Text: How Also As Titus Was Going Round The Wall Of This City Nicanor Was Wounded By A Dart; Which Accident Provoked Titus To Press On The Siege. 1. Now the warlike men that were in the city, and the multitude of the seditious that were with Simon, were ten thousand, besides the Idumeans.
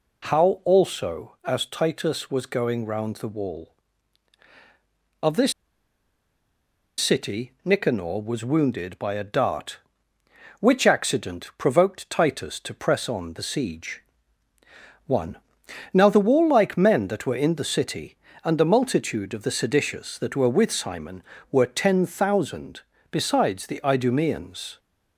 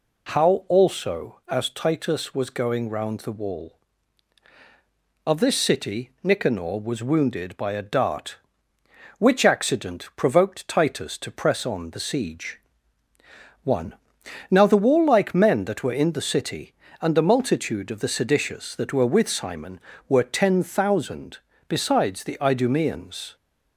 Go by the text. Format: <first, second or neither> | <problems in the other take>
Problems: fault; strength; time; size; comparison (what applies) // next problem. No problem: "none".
second | pauses between "This" and "City"; strong; at 5.5 s; 1.4 s long